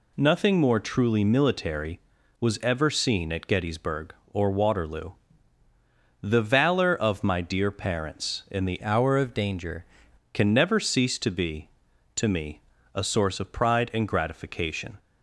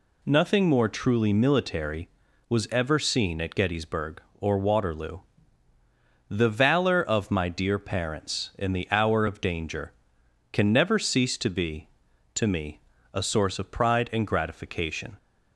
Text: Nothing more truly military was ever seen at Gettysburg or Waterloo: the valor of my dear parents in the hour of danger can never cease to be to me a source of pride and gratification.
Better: second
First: changes voice from "hour" to "danger"; from 8.8 to 9.8 s; 1.0 s long // pauses between "me" and "a"; slight; at 12.6 s; 0.34 s long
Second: pauses between "me" and "a"; slight; at 12.8 s; 0.34 s long

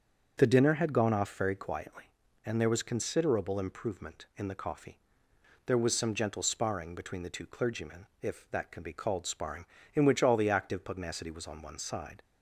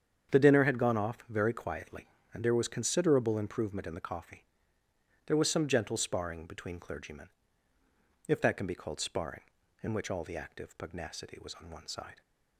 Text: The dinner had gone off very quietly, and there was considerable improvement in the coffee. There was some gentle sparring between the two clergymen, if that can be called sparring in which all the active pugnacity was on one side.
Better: first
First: starts louder than the rest; until 1.3 s; 6.5 dB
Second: starts louder than the rest; strong; until 1.3 s; 8 dB // skips "the two"; at 6.7 s

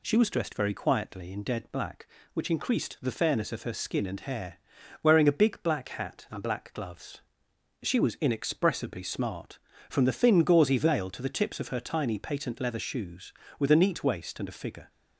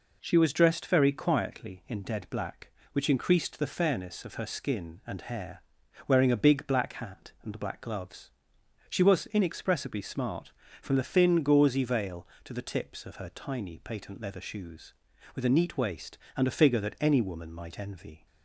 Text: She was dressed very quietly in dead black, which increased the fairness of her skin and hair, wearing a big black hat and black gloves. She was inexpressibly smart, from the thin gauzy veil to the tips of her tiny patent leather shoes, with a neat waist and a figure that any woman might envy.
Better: second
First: stops before "that any woman might envy"; at 14.8 s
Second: none

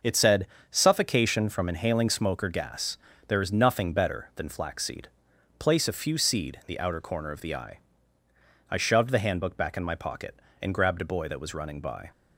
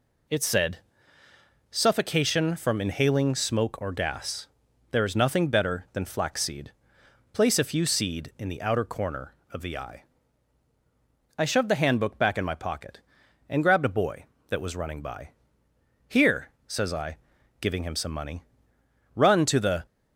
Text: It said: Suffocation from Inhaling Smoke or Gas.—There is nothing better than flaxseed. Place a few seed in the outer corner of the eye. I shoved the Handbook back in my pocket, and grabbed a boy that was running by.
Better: first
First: none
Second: goes on to say "Here says I giving him some money run to the"; strong; from 16.0 s on; 3.7 s long

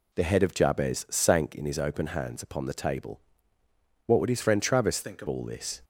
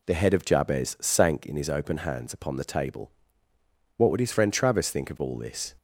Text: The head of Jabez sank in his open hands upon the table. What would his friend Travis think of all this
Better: second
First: changes voice from "think" to "of"; from 5.0 to 5.2 s; 0.2 s long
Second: none

